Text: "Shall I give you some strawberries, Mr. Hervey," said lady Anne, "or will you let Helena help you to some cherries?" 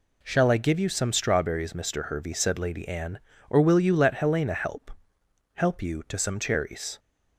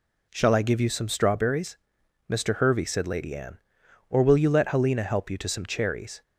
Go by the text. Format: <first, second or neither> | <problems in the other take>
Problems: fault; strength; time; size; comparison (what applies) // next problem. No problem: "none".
second | says "help" twice; at 5.5 s